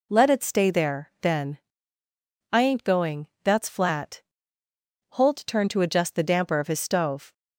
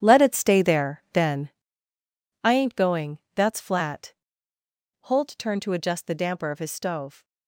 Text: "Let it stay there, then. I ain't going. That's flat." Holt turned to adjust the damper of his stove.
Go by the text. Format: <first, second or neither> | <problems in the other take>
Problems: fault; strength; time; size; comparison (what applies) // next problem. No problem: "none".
first | gets quieter; strong; throughout; 12 dB